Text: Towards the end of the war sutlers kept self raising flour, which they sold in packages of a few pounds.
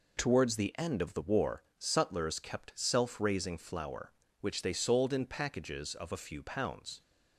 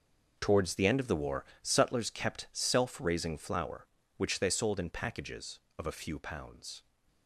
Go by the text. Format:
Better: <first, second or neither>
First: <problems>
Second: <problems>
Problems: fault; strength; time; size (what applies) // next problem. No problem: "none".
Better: first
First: pauses between "war" and "sutlers"; slight; at 1.6 s; 0.16 s long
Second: gets quieter; strong; throughout; 13.5 dB // pauses between "war" and "sutlers"; slight; at 1.4 s; 0.20 s long